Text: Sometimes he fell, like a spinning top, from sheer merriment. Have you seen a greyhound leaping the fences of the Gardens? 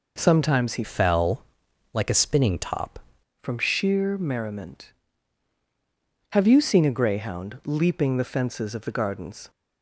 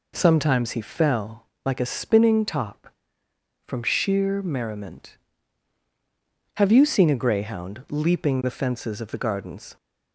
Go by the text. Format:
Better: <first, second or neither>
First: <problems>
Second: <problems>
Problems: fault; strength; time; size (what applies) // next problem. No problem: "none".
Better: second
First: changes voice from "fell" to "top"; from 0.8 to 2.9 s; 2.1 s long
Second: none